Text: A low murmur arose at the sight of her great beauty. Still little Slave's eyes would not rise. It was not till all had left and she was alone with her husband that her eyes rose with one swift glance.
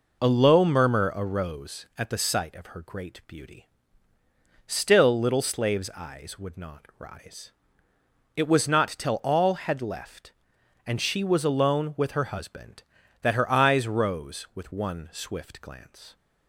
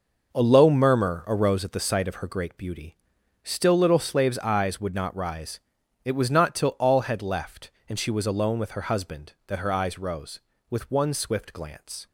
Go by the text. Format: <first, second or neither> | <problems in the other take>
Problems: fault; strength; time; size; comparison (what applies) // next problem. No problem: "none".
neither | none